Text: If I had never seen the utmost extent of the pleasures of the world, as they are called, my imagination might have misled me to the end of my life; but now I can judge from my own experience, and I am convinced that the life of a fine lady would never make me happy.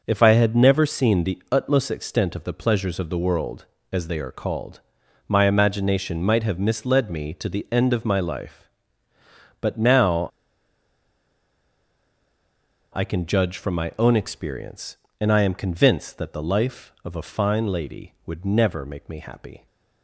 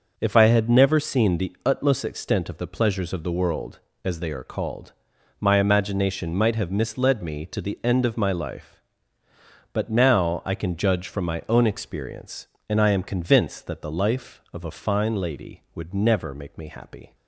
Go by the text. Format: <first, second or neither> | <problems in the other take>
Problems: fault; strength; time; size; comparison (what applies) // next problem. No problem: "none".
second | starts louder than the rest; noticeable; until 1.0 s; 6 dB // pauses between "now" and "I"; strong; at 10.2 s; 2.6 s long